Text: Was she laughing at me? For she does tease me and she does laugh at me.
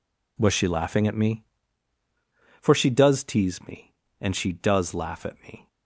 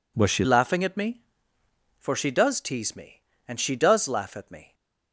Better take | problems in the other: first | changes voice at "laughing"; from 0.4 s on; 4.3 s long

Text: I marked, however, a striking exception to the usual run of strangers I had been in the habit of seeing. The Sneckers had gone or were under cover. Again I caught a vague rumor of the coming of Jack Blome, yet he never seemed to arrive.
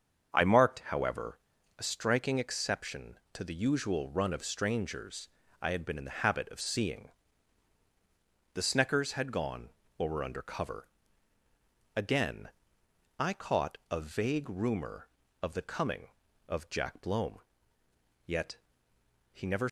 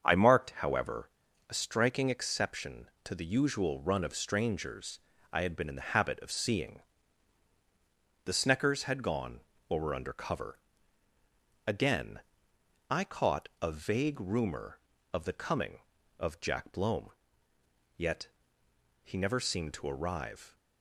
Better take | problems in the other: second | starts louder than the rest; until 1.8 s; 7 dB; also in the second // pauses between "strangers" and "I"; slight; at 5.2 s; 0.34 s long; slight in the second // pauses between "Again" and "I"; noticeable; at 12.4 s; 0.72 s long; noticeable in the second // pauses between "yet" and "he"; noticeable; at 18.5 s; 0.78 s long; noticeable in the second // stops before "seemed to arrive"; at 19.6 s

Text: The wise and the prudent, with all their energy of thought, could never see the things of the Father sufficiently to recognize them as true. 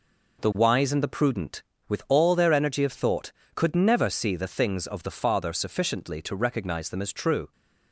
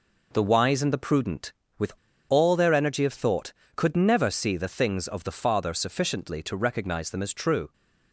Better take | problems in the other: first | pauses between "with" and "all"; at 1.9 s; 0.37 s long

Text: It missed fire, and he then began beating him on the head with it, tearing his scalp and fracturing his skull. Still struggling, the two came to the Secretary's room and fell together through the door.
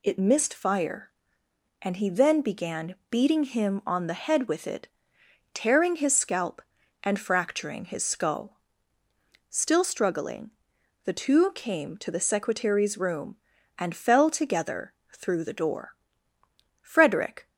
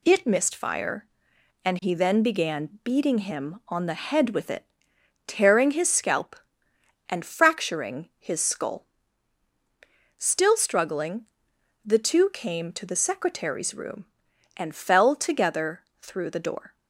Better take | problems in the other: second | pauses between "together" and "through"; slight; at 14.9 s; 0.18 s long; slight in the second // goes on to say "Frederick"; noticeable; from 16.8 s on; 0.68 s long

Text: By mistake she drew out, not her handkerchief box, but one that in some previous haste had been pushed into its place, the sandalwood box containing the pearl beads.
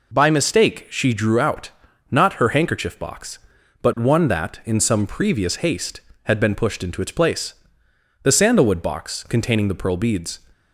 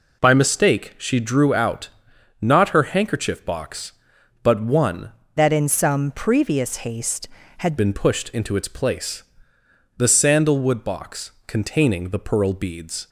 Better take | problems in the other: first | changes voice from "that" to "had"; from 5.3 to 7.7 s; 2.4 s long // pauses between "box" and "containing"; slight; at 11.3 s; 0.16 s long

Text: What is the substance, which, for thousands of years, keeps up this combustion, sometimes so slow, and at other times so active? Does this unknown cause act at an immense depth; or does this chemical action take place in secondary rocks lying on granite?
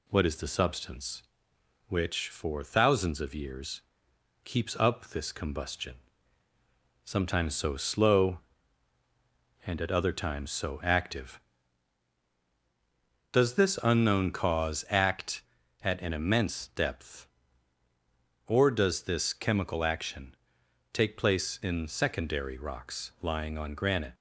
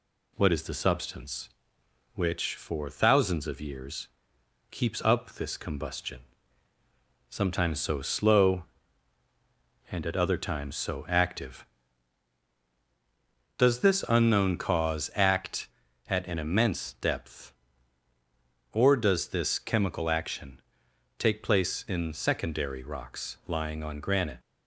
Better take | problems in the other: neither | pauses between "action" and "take"; noticeable; the same in both

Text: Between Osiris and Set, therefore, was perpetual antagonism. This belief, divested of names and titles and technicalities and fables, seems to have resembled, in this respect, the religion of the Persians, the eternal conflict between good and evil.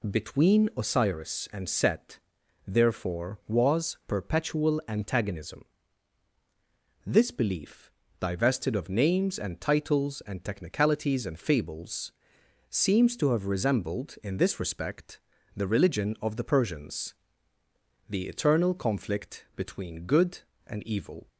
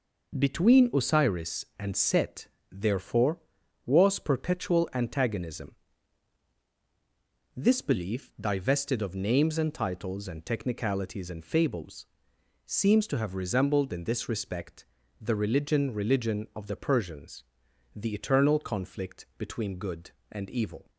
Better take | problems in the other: first | says "religion" twice; at 15.9 s

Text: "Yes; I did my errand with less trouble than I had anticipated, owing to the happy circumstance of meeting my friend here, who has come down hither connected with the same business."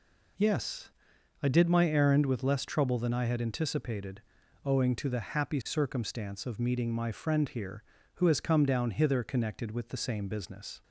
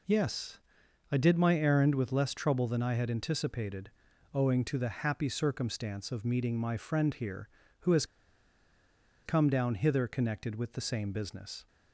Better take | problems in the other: first | pauses between "has" and "come"; at 8.0 s; 1.2 s long

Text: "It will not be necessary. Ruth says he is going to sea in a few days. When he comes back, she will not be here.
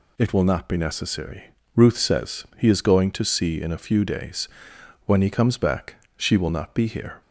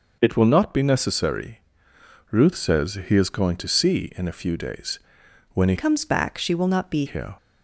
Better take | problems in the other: first | changes voice from "comes" to "be"; from 5.7 to 7.0 s; 1.3 s long

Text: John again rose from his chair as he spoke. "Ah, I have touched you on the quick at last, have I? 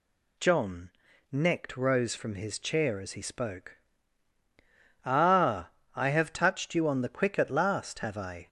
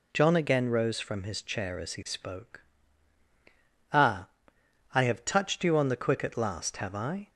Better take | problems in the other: second | says "necked" for "again"; at 1.3 s

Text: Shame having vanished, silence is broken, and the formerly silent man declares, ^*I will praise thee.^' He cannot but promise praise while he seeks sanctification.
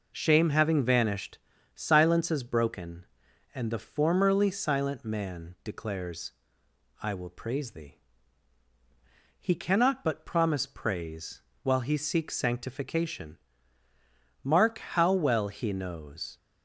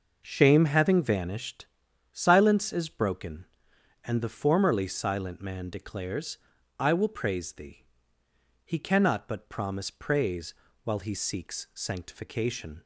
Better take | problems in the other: second | pauses between "praise" and "while"; slight; at 11.4 s; 0.22 s long; slight in the second // goes on to say "Mark how well he knows"; strong; from 14.4 s on; 1.9 s long

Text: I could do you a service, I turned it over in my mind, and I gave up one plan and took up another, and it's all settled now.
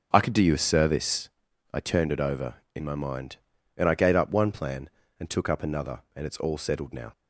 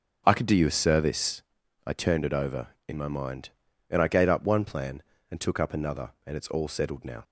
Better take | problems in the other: neither | starts louder than the rest; the same in both

